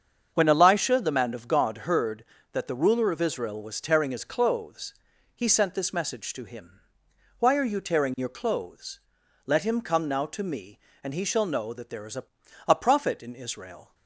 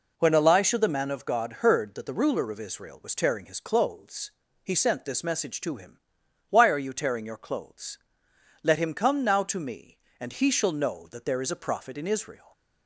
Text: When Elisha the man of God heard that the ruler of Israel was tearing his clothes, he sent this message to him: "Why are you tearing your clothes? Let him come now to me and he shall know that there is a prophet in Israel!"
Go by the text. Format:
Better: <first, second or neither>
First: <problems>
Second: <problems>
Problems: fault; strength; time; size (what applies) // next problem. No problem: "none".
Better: second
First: starts louder than the rest; strong; until 1.3 s; 7 dB // says "a" twice; at 12.6 s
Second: none